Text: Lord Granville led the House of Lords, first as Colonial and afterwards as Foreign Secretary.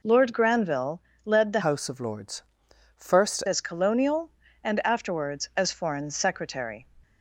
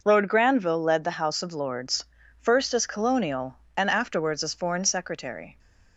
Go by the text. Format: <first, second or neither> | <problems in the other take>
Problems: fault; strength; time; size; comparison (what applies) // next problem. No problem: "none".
second | pauses between "Granville" and "led"; slight; at 0.9 s; 0.24 s long // changes voice from "House" to "first"; from 1.6 to 3.4 s; 1.8 s long